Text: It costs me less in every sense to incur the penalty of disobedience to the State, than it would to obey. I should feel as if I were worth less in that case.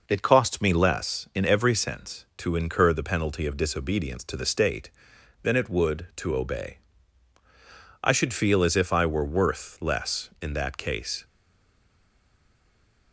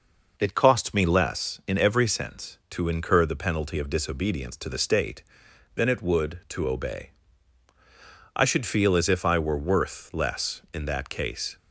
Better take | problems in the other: second | stays silent after the last word; noticeable; from 11.2 s on; 1.9 s long

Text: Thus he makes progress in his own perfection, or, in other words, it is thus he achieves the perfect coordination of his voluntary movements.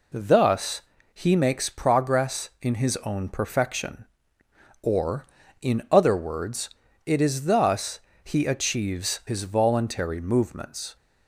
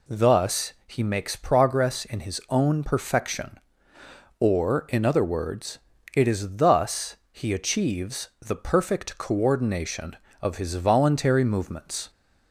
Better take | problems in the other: second | pauses between "Thus" and "he"; slight; at 0.8 s; 0.32 s long // pauses between "thus" and "he"; slight; at 7.9 s; 0.24 s long; slight in the second // skips "the perfect coordination of"; at 9.2 s

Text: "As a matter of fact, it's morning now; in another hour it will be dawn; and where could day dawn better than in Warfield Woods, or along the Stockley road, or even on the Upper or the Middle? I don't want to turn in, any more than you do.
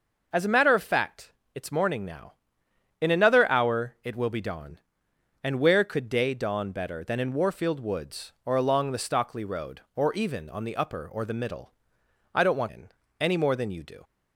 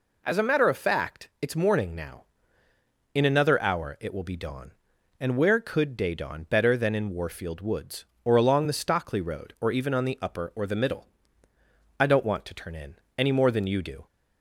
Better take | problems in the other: second | skips "to turn"; at 12.6 s

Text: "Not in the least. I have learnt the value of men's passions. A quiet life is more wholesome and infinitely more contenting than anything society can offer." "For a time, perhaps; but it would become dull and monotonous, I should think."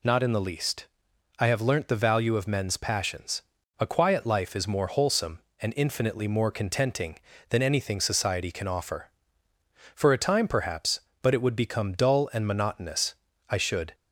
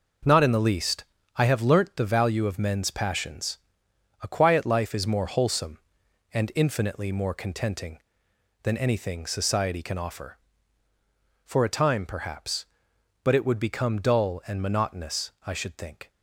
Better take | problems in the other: second | stops before "think"; at 13.9 s

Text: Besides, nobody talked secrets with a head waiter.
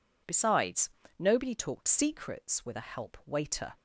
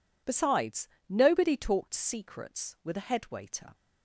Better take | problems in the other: second | says "help" for "head"; at 2.9 s

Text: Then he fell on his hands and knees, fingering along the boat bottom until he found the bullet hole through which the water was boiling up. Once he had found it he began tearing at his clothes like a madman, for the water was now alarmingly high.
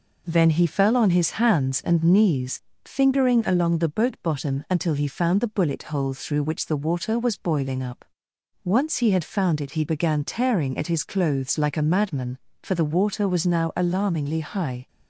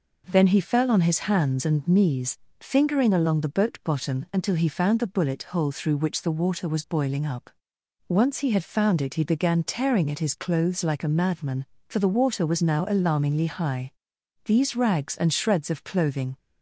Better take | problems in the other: first | goes on to say "These rags and shreds of clothing"; strong; from 14.4 s on; 1.9 s long

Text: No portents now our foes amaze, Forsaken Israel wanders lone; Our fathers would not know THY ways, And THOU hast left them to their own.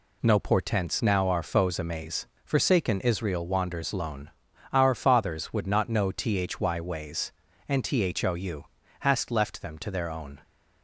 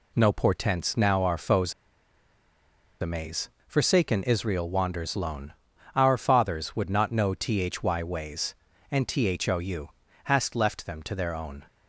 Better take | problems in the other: first | pauses between "foes" and "amaze"; strong; at 1.7 s; 1.2 s long // pauses between "THOU" and "hast"; slight; at 9.8 s; 0.36 s long; slight in the first

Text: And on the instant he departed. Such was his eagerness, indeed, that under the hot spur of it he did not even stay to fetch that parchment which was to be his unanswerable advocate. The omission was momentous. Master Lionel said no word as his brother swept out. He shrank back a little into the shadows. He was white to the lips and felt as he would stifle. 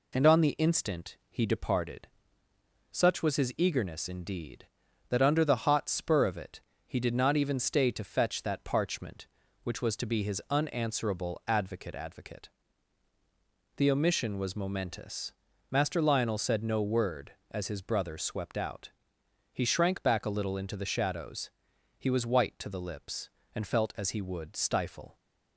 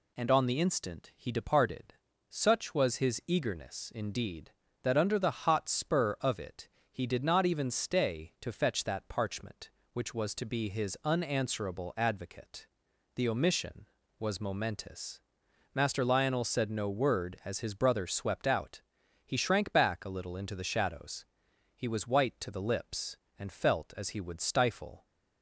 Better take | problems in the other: second | pauses between "it" and "he"; slight; at 6.5 s; 0.26 s long; slight in the second // says "advocate" twice; at 11.9 s

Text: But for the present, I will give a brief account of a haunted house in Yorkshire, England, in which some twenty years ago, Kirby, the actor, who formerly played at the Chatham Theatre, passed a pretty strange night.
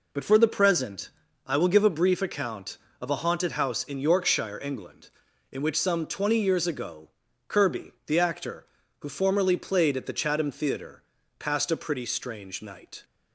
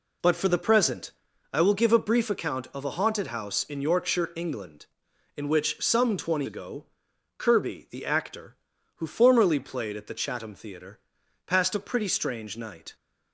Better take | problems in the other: first | skips "years"; at 6.4 s

